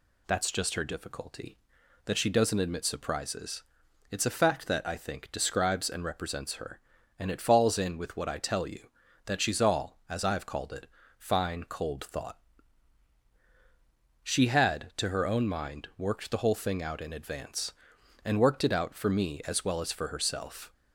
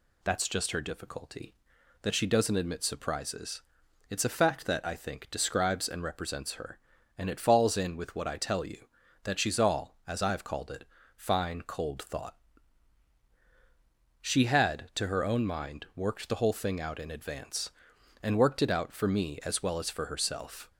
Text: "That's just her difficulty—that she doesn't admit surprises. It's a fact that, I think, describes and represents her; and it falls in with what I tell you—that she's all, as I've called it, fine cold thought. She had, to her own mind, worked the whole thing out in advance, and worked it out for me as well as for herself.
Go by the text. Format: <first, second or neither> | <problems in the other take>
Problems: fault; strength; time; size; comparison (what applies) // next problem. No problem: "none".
neither | none